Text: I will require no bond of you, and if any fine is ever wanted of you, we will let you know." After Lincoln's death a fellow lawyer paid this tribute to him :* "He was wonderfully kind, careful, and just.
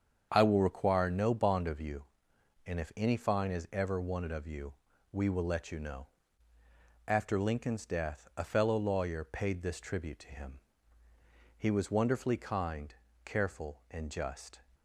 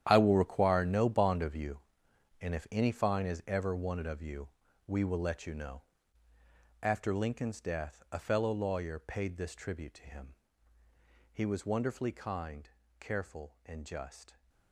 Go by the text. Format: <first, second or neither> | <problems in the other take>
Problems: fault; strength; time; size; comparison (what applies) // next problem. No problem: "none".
first | gets quieter; strong; throughout; 15 dB // starts louder than the rest; strong; until 1.0 s; 10.5 dB; strong in the first